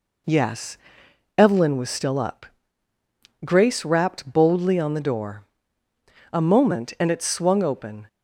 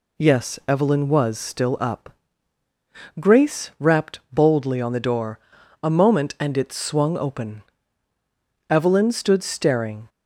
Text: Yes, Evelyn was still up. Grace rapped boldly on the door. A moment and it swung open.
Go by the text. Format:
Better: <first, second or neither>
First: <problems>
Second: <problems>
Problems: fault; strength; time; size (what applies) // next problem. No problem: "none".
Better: first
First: none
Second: goes on to say "Evelyn stood staring"; from 8.7 s on; 1.3 s long